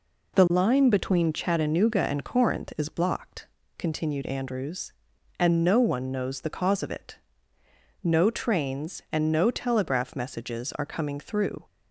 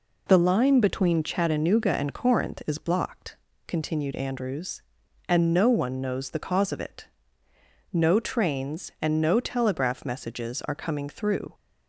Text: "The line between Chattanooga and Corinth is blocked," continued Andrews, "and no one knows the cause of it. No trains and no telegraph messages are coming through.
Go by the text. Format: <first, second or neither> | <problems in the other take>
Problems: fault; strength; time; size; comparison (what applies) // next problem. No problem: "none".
neither | none